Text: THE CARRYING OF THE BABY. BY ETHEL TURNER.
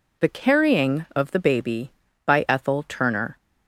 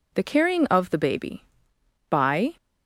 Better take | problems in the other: first | stops before "ETHEL TURNER"; at 2.5 s

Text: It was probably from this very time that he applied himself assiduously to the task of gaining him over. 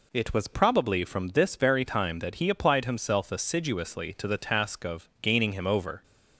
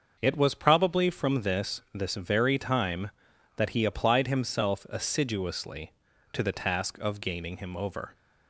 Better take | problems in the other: first | starts louder than the rest; until 1.2 s; 6 dB // says "this" twice; at 1.9 s

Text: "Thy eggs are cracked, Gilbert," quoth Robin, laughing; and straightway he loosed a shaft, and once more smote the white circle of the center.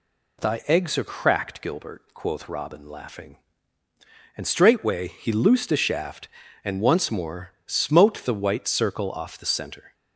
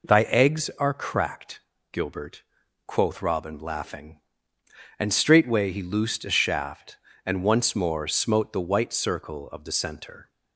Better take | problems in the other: second | says "off" for "of"; at 9.1 s

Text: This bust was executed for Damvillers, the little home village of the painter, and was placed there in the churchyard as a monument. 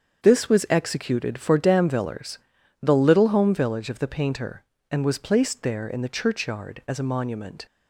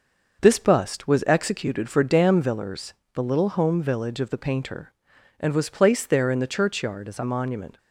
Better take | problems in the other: second | starts louder than the rest; strong; until 1.2 s; 7.5 dB; noticeable in the second // skips "bust"; at 0.4 s

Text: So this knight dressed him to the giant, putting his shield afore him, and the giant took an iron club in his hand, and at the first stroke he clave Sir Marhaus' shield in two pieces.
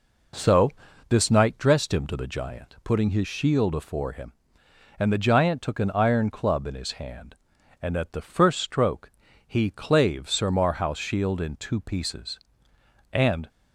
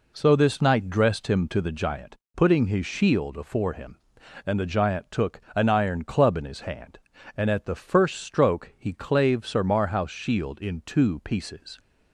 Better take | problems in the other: second | pauses between "So" and "this"; at 0.7 s; 0.38 s long // pauses between "stroke" and "he"; slight; at 9.1 s; 0.36 s long // goes on to say "And"; slight; from 13.1 s on; 0.36 s long

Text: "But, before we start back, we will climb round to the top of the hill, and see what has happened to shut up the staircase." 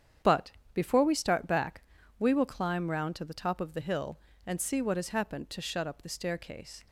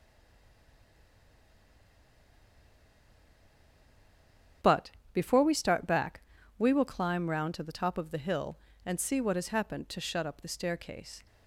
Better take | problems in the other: first | stays silent before the first word; strong; until 4.6 s; 4.6 s long // starts louder than the rest; strong; until 5.8 s; 8.5 dB; strong in the first

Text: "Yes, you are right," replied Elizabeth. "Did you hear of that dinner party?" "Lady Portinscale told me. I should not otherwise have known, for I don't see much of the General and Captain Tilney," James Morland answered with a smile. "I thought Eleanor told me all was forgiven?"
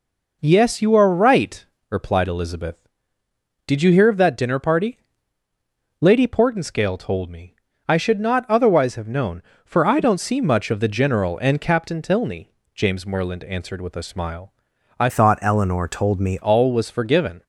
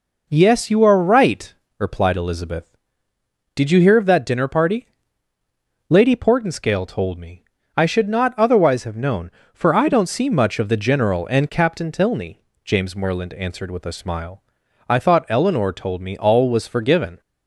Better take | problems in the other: second | changes voice from "thought" to "me"; from 15.0 to 16.3 s; 1.3 s long

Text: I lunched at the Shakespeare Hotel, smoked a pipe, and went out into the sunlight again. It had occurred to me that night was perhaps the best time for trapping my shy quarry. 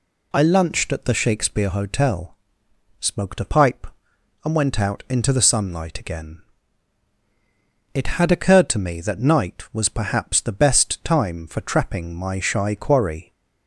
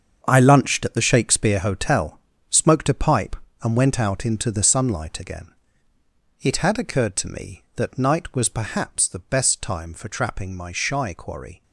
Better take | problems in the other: first | gets quieter; strong; throughout; 11.5 dB

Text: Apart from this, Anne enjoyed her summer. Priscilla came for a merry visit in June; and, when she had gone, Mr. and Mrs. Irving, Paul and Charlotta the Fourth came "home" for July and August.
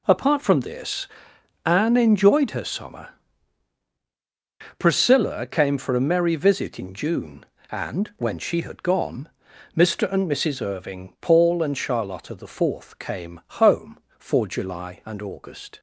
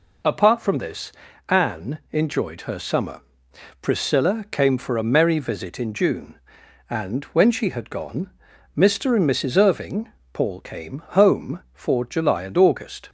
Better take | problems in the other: first | skips "and Charlotta the Fourth"; at 10.5 s // pauses between "came" and "home"; slight; at 11.0 s; 0.16 s long; slight in the first

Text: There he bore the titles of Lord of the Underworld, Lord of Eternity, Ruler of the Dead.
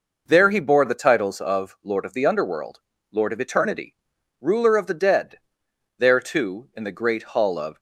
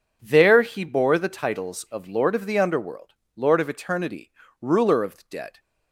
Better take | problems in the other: second | goes on to say "There too in the great Hall of"; strong; from 5.9 s on; 1.8 s long

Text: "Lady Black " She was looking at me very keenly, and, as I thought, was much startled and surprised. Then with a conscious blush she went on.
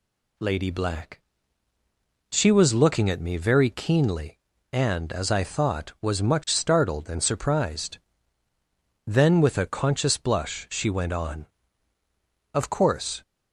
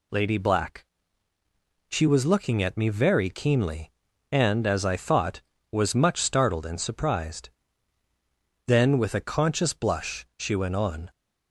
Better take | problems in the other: second | goes on to say "Of course"; noticeable; from 12.5 s on; 0.68 s long

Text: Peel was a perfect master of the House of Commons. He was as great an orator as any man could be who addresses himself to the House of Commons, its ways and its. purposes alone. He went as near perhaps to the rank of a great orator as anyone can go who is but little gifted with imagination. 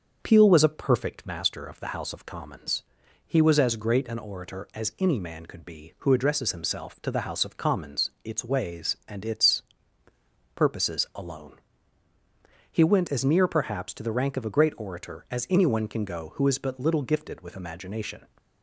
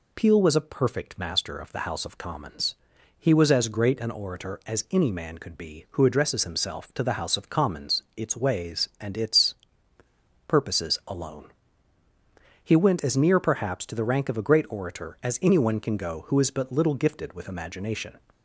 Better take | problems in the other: second | starts louder than the rest; until 1.2 s; 6.5 dB

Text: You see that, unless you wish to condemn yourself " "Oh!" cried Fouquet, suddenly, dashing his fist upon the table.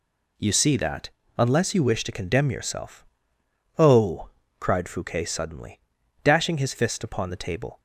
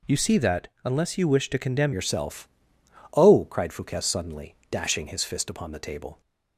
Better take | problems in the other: first | changes voice at "yourself"; from 1.9 s on; 4.3 s long

